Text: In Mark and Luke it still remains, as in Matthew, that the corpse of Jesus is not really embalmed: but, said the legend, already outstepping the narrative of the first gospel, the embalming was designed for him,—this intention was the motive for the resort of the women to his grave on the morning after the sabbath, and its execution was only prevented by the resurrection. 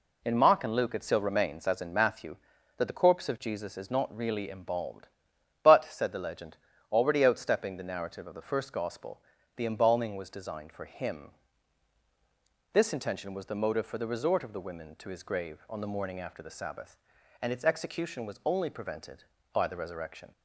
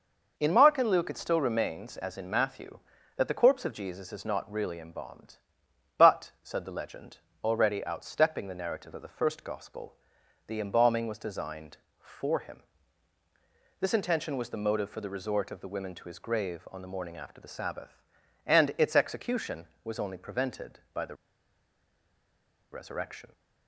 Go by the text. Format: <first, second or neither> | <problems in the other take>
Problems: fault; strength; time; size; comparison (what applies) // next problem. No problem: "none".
first | pauses between "the" and "resurrection"; strong; at 21.1 s; 1.5 s long